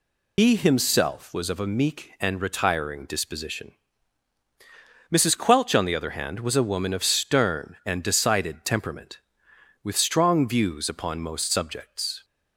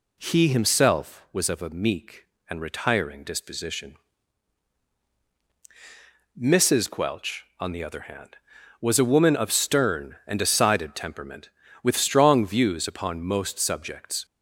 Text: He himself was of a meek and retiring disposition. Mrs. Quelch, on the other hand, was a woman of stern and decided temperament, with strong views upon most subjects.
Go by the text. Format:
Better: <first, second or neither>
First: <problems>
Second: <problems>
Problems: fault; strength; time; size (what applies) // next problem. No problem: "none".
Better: second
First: loses the start of "He"; at 0.3 s; 75 ms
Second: none